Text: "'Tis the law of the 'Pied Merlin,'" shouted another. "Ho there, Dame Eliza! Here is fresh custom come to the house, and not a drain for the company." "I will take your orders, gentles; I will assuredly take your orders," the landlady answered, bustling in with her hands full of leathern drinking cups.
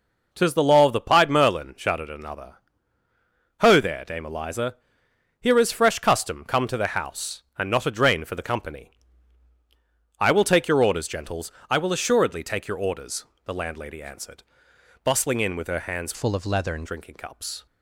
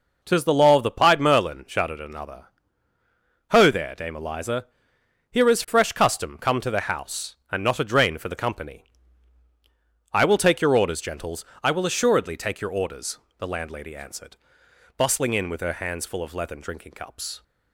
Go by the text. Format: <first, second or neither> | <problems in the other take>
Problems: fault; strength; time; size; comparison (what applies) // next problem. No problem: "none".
second | changes voice from "full" to "leathern"; from 16.1 to 16.8 s; 0.7 s long